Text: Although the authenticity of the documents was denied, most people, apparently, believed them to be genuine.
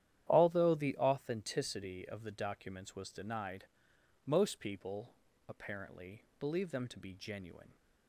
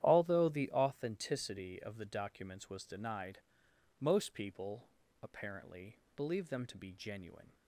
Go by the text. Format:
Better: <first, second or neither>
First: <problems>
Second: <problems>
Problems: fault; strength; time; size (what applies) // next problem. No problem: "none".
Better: neither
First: starts louder than the rest; strong; until 1.3 s; 11 dB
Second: starts louder than the rest; strong; until 1.0 s; 11 dB